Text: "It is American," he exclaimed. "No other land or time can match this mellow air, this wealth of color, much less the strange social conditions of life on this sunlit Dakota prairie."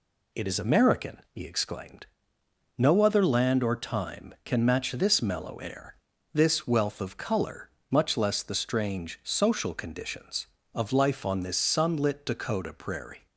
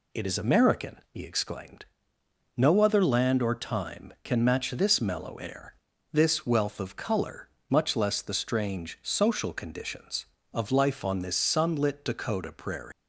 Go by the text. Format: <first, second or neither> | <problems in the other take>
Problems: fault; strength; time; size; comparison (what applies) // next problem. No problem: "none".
first | leaves "prairie" unfinished; at 12.9 s; 130 ms